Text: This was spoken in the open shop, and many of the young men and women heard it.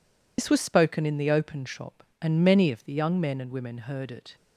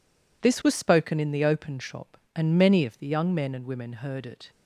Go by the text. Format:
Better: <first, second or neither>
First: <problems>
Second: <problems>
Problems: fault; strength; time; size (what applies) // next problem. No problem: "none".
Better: second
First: loses the start of "This"; at 0.3 s; 85 ms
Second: none